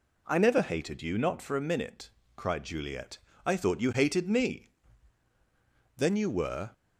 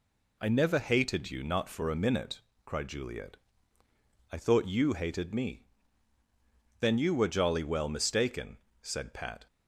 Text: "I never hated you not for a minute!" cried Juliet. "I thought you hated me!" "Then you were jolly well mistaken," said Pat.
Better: second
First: stops before "jolly well mistaken said Pat"; at 6.7 s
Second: none

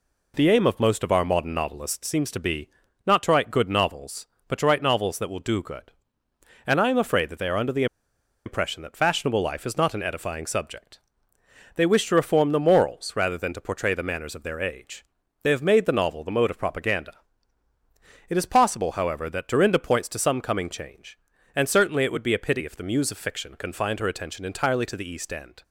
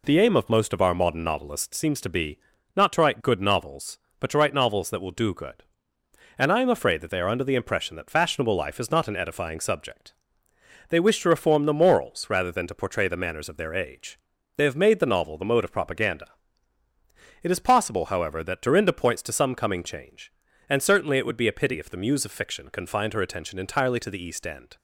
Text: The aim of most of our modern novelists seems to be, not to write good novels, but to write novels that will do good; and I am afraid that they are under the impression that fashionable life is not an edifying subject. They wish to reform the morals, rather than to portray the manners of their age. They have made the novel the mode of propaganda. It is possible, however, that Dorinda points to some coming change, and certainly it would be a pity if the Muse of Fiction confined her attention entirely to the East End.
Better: second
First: pauses between "the" and "impression"; noticeable; at 7.8 s; 0.60 s long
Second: none

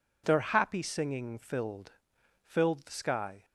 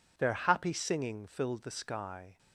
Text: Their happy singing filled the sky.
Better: second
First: says "filled" twice; at 2.4 s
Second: none

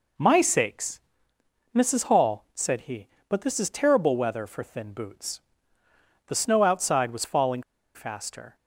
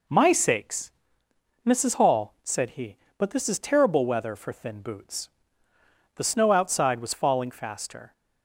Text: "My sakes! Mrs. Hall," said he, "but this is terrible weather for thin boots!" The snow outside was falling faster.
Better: second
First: pauses between "falling" and "faster"; slight; at 7.6 s; 0.33 s long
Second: none

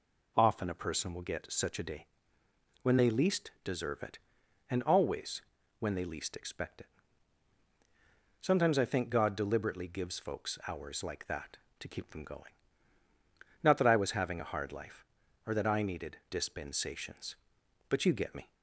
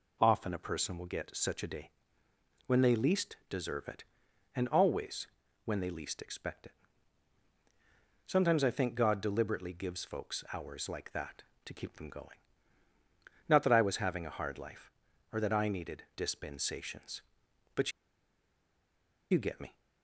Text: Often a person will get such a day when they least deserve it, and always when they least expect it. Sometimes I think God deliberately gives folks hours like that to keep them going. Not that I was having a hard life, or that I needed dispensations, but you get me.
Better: first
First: pauses between "day" and "when"; noticeable; at 2.0 s; 0.76 s long // pauses between "always" and "when"; at 5.4 s; 0.38 s long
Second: pauses between "day" and "when"; noticeable; at 1.9 s; 0.76 s long // pauses between "always" and "when"; at 5.2 s; 0.38 s long // pauses between "but" and "you"; strong; at 17.9 s; 1.3 s long

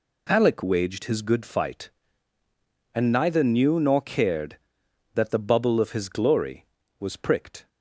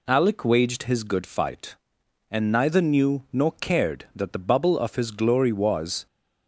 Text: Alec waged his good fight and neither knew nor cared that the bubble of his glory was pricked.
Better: first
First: none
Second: stops before "pricked"; at 6.0 s

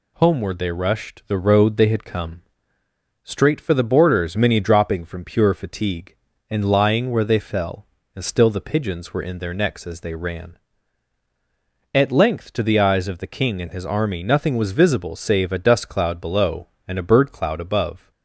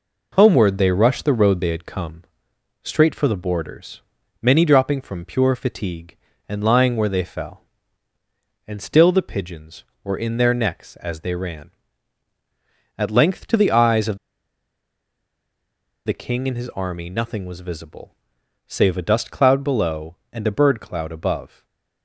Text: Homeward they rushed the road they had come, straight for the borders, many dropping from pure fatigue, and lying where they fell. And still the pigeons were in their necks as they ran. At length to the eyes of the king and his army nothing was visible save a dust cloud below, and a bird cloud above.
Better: first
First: none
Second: pauses between "of" and "the"; strong; at 14.1 s; 1.8 s long // pauses between "visible" and "save"; noticeable; at 18.1 s; 0.54 s long // stays silent after the last word; slight; from 21.4 s on; 0.6 s long

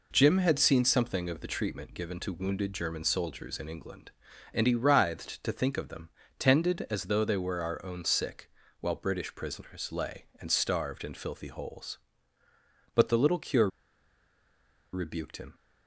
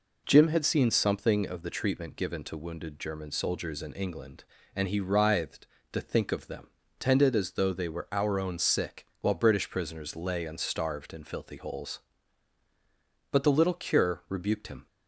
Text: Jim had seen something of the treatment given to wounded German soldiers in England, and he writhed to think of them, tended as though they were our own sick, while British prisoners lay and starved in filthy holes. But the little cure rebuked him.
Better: second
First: pauses between "cure" and "rebuked"; at 13.6 s; 1.2 s long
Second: none

